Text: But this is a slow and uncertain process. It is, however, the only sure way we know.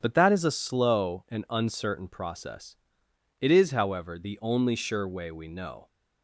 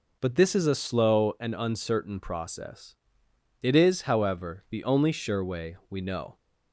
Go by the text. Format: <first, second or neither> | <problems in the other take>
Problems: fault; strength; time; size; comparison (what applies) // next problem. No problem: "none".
second | starts louder than the rest; strong; until 1.0 s; 8 dB // says "that" for "this"; at 0.1 s